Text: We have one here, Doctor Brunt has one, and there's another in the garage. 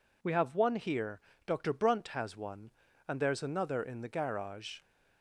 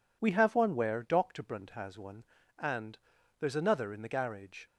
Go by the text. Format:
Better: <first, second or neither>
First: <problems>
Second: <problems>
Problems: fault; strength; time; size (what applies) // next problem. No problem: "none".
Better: first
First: none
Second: says "where" for "here"; at 0.7 s // pauses between "and" and "there's"; at 2.9 s; 0.40 s long